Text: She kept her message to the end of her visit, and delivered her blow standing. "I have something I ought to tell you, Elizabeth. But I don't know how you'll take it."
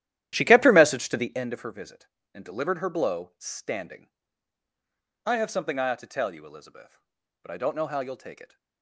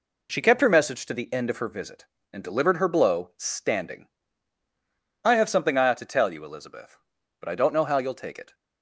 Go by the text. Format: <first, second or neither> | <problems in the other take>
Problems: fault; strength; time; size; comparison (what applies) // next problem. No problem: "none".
second | starts louder than the rest; strong; until 1.5 s; 12 dB